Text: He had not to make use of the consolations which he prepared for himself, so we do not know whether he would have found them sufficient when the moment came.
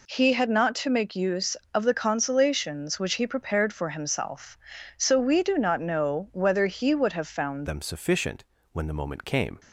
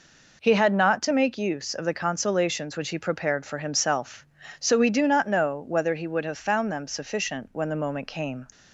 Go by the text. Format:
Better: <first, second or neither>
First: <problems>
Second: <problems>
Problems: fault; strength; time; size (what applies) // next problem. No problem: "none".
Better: second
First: changes voice at "them"; from 7.6 s on; 1.9 s long // pauses between "sufficient" and "when"; slight; at 8.4 s; 0.28 s long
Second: none